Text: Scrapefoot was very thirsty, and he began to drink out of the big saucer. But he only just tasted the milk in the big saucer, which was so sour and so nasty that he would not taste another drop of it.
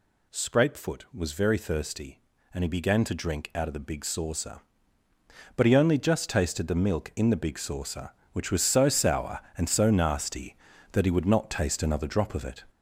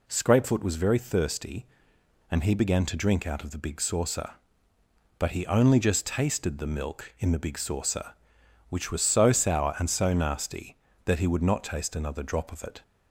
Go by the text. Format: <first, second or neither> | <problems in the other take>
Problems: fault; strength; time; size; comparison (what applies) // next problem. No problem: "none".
second | gets louder; noticeable; throughout; 5 dB